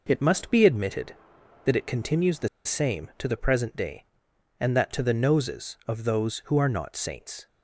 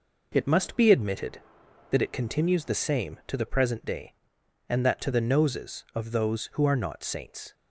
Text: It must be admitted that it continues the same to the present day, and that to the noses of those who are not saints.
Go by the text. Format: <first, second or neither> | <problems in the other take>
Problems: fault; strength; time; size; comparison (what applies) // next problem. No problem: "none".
second | pauses between "the" and "same"; slight; at 2.4 s; 0.17 s long